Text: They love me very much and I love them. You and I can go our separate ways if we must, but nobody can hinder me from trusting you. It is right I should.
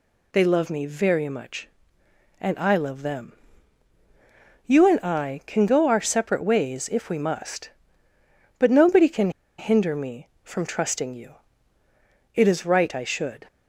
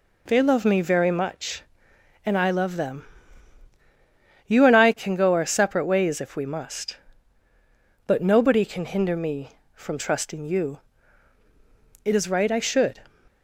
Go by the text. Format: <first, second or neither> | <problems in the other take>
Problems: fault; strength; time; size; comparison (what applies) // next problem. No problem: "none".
second | pauses between "can" and "hinder"; slight; at 9.3 s; 0.27 s long